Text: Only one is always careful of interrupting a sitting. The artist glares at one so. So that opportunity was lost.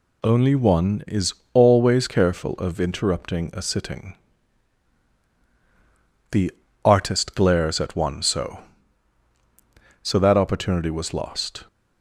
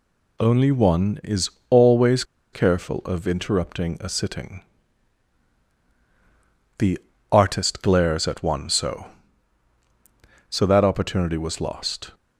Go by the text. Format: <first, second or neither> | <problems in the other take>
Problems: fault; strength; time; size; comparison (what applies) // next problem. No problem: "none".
first | pauses between "is" and "always"; slight; at 1.4 s; 0.22 s long; slight in the first // pauses between "always" and "careful"; slight; at 2.2 s; 0.30 s long // pauses between "The" and "artist"; slight; at 6.9 s; 0.32 s long; slight in the first